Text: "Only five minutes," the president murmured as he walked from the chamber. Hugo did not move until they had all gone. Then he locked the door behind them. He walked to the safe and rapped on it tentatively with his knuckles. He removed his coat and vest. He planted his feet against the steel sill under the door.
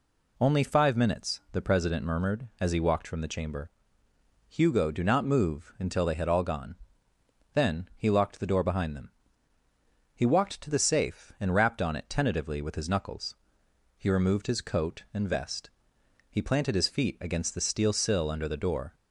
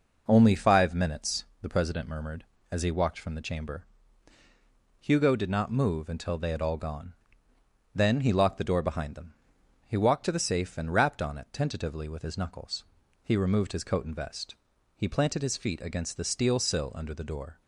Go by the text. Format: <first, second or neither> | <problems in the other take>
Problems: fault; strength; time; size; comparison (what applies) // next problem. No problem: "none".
second | says "do" for "did"; at 4.8 s